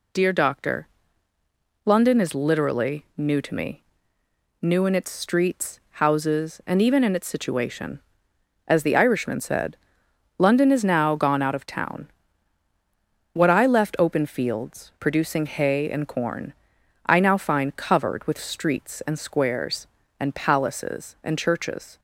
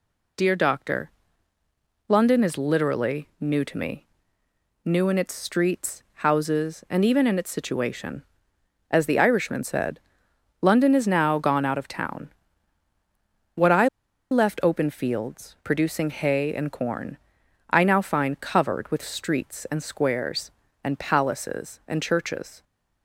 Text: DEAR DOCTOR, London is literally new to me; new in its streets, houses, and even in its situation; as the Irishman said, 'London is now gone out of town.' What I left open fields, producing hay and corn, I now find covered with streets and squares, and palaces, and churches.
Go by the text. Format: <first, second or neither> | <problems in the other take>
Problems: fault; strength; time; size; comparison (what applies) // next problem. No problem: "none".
first | pauses between "I" and "left"; at 13.8 s; 0.42 s long